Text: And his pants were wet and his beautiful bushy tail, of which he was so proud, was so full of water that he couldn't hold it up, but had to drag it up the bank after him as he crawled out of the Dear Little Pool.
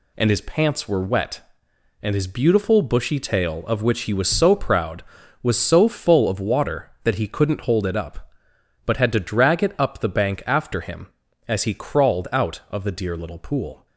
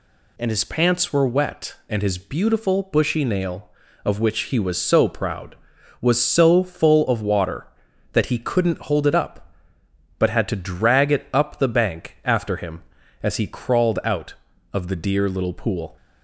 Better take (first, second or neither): first